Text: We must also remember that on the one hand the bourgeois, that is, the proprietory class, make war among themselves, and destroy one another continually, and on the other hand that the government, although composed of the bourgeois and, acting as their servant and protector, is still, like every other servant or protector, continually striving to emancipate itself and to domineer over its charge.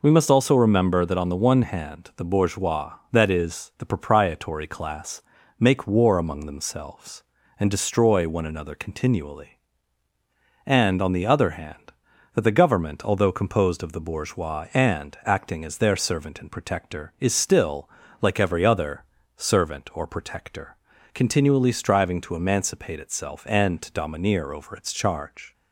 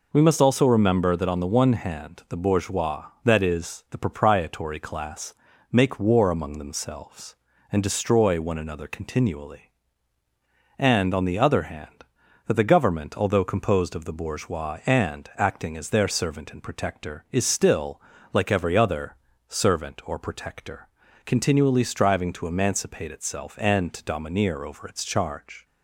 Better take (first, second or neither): neither